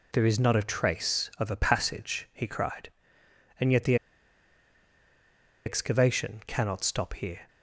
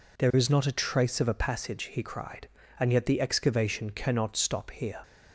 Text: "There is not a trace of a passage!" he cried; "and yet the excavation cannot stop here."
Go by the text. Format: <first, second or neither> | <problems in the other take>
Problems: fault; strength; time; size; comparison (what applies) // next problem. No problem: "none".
second | pauses between "the" and "excavation"; strong; at 3.9 s; 1.7 s long